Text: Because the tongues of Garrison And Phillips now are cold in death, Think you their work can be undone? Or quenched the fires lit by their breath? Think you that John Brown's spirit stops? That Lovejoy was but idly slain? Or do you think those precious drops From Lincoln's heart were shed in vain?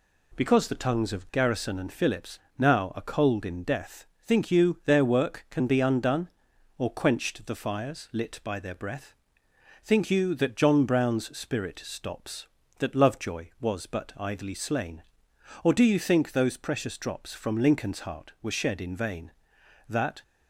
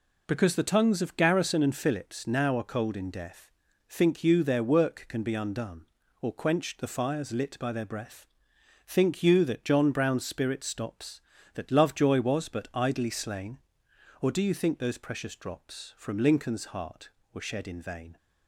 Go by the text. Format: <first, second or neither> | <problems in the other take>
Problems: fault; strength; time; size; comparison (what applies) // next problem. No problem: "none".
second | pauses between "Phillips" and "now"; slight; at 2.3 s; 0.20 s long // goes on to say "That"; slight; from 19.8 s on; 0.34 s long